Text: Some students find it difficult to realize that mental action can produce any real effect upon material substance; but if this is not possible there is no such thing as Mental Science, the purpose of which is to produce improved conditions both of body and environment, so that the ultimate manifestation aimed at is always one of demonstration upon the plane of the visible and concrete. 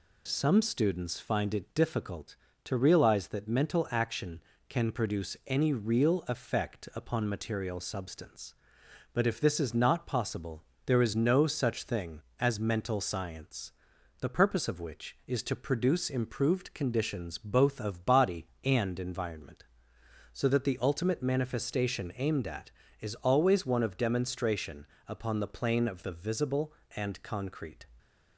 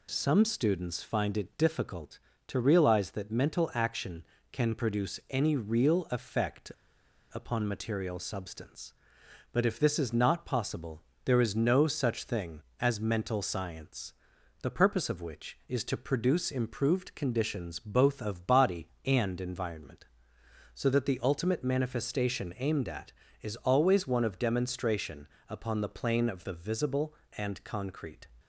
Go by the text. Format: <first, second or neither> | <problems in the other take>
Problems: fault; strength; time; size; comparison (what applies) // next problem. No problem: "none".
first | pauses between "effect" and "upon"; noticeable; at 6.7 s; 0.63 s long // pauses between "possible" and "there"; slight; at 11.0 s; 0.22 s long; slight in the first // pauses between "demonstration" and "upon"; slight; at 25.2 s; 0.20 s long; slight in the first